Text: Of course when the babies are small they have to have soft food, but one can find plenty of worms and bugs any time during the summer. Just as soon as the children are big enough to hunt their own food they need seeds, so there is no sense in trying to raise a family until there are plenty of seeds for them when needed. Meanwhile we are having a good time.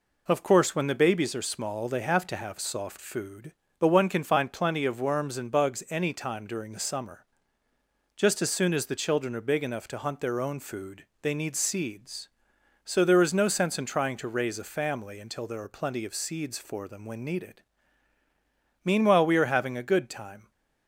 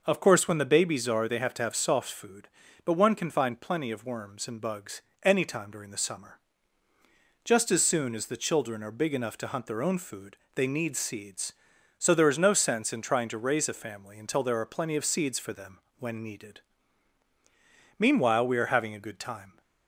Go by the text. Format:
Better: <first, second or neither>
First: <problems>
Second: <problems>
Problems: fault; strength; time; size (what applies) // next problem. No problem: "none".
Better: first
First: pauses between "food" and "they"; slight; at 11.0 s; 0.18 s long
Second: skips "small"; at 1.2 s // pauses between "bugs" and "any"; slight; at 5.0 s; 0.20 s long // pauses between "food" and "they"; slight; at 10.3 s; 0.16 s long // pauses between "them" and "when"; slight; at 15.8 s; 0.18 s long